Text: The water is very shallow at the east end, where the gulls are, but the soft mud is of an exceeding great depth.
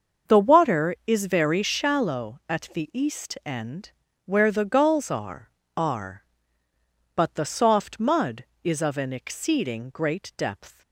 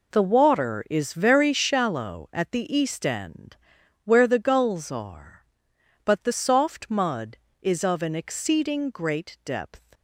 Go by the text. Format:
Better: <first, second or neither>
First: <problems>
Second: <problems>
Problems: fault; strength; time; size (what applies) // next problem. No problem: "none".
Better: second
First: starts louder than the rest; until 1.3 s; 6.5 dB // says "are" twice; at 5.7 s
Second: none